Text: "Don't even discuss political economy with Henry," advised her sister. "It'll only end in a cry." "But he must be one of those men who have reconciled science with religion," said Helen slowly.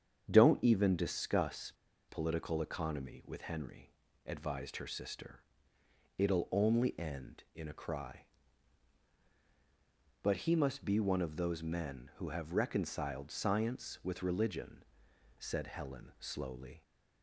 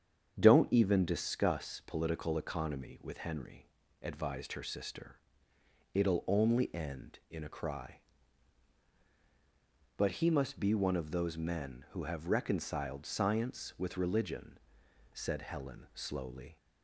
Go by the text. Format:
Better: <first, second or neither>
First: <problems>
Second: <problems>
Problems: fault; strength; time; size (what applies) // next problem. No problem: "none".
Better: second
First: starts louder than the rest; strong; until 1.2 s; 7.5 dB // pauses between "discuss" and "political"; at 1.7 s; 0.38 s long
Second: starts louder than the rest; strong; until 1.3 s; 7.5 dB